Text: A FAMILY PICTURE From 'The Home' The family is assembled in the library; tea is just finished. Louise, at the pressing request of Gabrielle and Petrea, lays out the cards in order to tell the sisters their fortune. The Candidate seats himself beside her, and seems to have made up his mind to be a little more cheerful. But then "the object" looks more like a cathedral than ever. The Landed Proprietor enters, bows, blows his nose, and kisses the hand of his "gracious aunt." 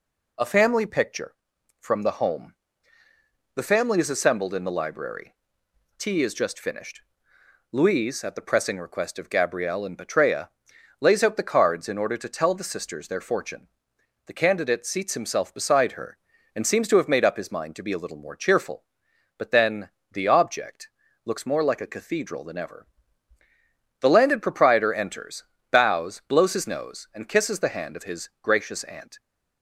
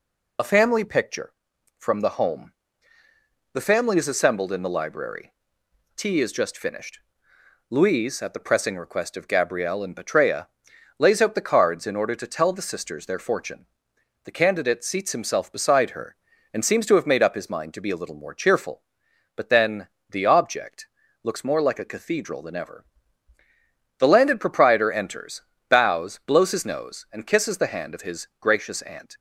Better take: first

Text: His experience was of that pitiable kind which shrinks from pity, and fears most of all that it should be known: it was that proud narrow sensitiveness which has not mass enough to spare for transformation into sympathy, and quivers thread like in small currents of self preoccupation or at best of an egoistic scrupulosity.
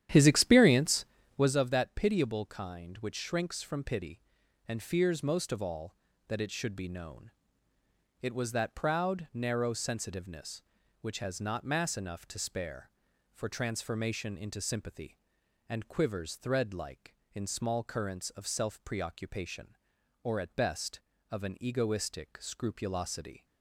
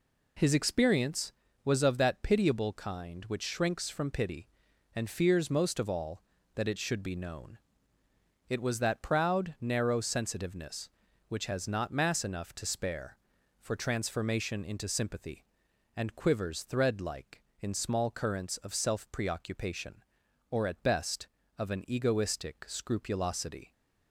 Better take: second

